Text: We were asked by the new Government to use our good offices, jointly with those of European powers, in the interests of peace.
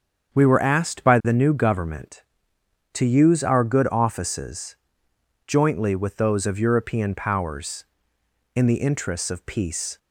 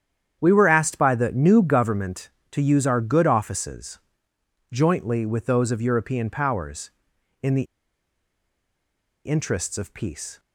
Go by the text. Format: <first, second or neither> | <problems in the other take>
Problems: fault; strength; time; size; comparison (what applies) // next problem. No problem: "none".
first | starts louder than the rest; strong; until 1.4 s; 9 dB; strong in the first // pauses between "the" and "interests"; strong; at 7.6 s; 1.6 s long